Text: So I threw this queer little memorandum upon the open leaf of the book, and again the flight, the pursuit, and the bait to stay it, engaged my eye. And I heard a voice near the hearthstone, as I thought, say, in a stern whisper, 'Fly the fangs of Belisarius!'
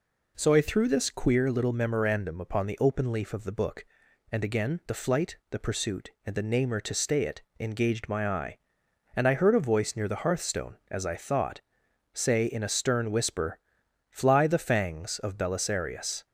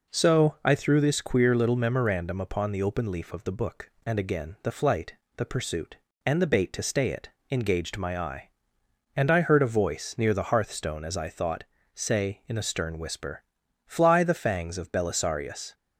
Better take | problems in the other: second | says "namer" for "bait"; at 6.4 s

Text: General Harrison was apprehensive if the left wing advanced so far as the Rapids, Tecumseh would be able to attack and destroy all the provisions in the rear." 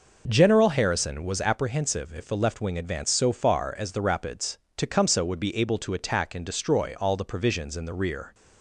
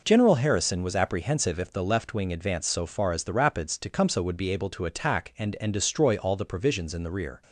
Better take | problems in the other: first | says "and" twice; at 5.6 s

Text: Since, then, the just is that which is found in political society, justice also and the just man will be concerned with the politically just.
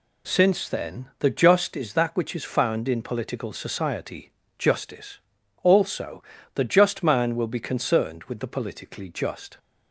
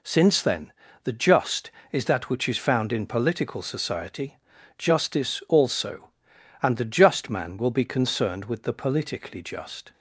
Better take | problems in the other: second | pauses between "justice" and "also"; at 5.1 s; 0.44 s long // skips "and"; at 6.3 s

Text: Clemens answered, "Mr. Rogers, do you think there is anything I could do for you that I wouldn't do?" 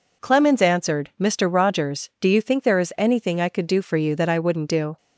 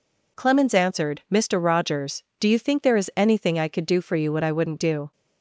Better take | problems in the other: first | says "what" for "that"; at 4.3 s

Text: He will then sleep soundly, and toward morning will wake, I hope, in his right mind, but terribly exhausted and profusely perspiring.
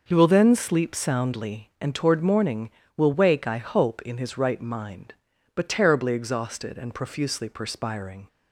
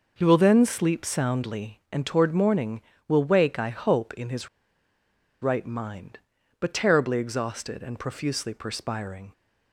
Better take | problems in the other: first | pauses between "his" and "right"; noticeable; at 4.4 s; 0.93 s long

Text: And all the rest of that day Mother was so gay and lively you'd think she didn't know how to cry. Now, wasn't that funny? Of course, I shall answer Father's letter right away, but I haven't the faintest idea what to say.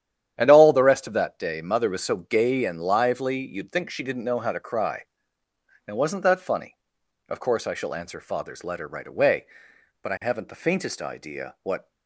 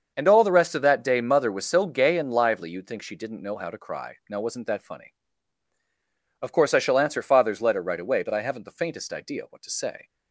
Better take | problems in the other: second | starts louder than the rest; strong; until 1.4 s; 10 dB; also in the second // stops before "to say"; at 11.9 s

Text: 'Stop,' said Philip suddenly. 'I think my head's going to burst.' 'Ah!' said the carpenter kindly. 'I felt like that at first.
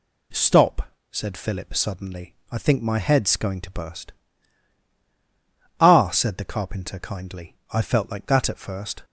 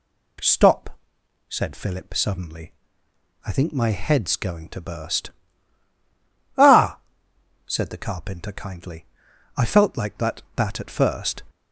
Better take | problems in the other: first | says "that" twice; at 10.5 s

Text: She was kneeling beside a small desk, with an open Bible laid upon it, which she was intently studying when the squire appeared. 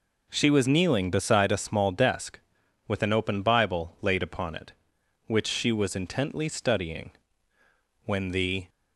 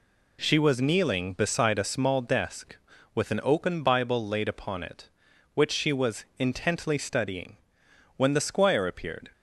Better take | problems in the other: second | pauses between "studying" and "when"; noticeable; at 7.1 s; 0.94 s long; noticeable in the second // stops before "squire appeared"; at 8.6 s

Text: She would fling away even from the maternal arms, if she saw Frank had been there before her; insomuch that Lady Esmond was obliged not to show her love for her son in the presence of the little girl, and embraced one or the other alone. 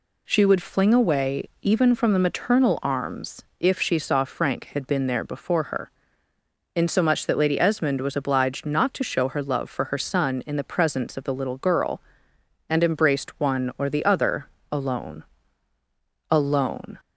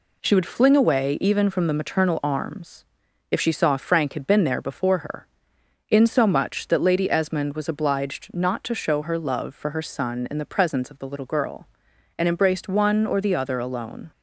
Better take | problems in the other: second | pauses between "other" and "alone"; slight; at 14.4 s; 0.24 s long // says "alone" twice; at 16.3 s

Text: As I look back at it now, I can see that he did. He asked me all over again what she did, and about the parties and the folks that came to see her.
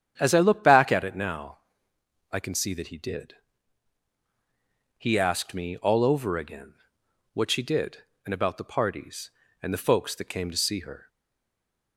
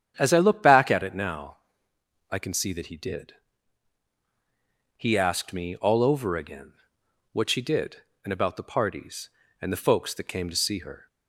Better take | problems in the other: second | starts louder than the rest; strong; until 1.2 s; 9 dB; strong in the second // pauses between "again" and "what"; noticeable; at 6.7 s; 0.58 s long; noticeable in the second // stays silent after the last word; slight; from 11.0 s on; 0.9 s long

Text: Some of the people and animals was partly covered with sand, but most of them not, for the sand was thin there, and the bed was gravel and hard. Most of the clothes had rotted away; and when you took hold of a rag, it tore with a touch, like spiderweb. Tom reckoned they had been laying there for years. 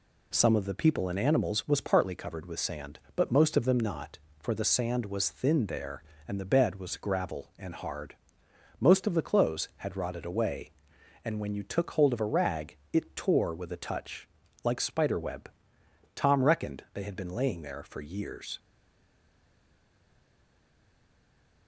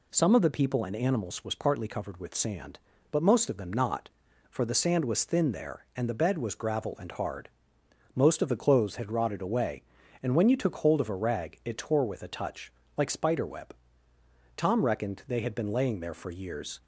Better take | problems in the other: second | stays silent after the last word; strong; from 18.5 s on; 3.1 s long

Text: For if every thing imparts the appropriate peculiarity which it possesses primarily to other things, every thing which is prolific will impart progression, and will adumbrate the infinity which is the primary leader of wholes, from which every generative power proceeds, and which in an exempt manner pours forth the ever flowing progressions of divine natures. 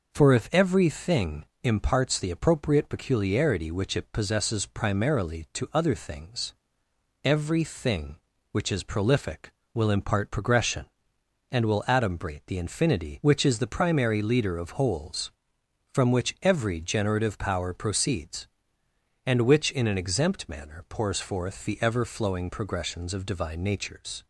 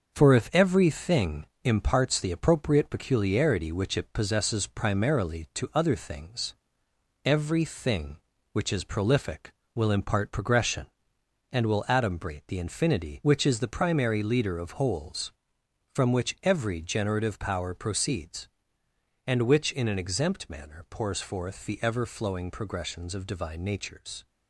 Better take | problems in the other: first | gets quieter; noticeable; throughout; 4 dB // pauses between "thing" and "imparts"; slight; at 1.4 s; 0.16 s long; slight in the first

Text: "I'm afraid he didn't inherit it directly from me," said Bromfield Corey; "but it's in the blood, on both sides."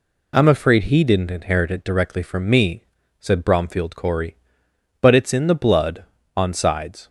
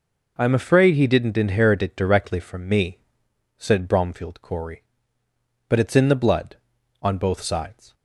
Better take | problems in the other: second | skips "both"; at 6.5 s

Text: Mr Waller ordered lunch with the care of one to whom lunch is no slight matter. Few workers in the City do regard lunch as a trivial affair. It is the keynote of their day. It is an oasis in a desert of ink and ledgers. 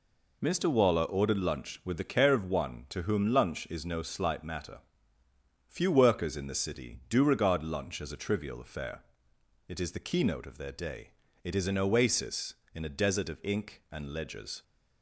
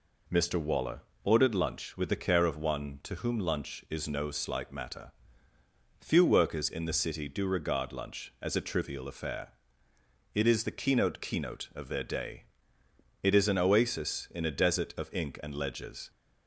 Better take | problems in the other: first | pauses between "Waller" and "ordered"; slight; at 1.0 s; 0.20 s long // says "keynote" twice; at 11.2 s

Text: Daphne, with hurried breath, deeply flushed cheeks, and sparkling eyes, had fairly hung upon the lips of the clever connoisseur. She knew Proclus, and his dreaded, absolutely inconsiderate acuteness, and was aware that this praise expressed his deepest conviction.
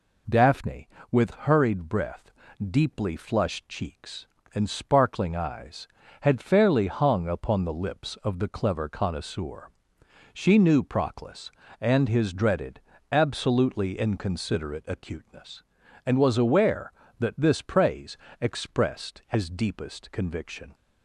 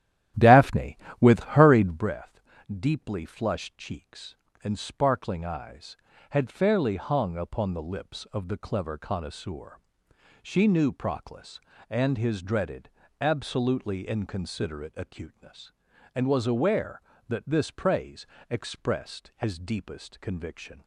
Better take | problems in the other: first | starts louder than the rest; strong; until 2.1 s; 12 dB // pauses between "praise" and "expressed"; slight; at 18.2 s; 0.22 s long; slight in the first

